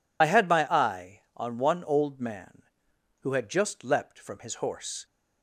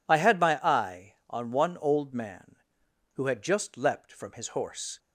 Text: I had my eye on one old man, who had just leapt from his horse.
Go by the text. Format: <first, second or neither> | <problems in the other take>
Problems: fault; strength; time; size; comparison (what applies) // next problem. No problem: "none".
second | loses the start of "I"; at 0.2 s; 35 ms